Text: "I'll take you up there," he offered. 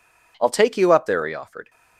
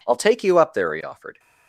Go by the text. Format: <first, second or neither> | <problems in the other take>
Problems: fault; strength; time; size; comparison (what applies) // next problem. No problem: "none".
neither | none